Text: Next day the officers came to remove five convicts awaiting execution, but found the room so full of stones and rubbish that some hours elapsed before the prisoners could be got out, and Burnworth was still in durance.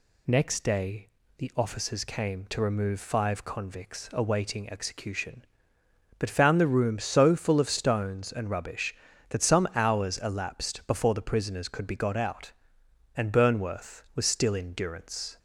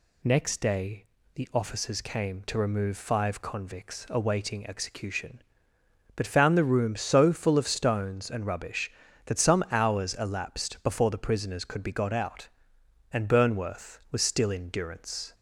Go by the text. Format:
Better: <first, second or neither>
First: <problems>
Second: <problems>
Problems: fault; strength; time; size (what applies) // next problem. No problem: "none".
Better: neither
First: pauses between "day" and "the"; slight; at 1.0 s; 0.30 s long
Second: pauses between "day" and "the"; slight; at 1.0 s; 0.30 s long